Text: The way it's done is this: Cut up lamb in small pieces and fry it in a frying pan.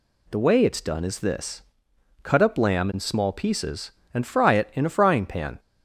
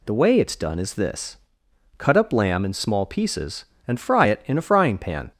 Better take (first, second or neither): neither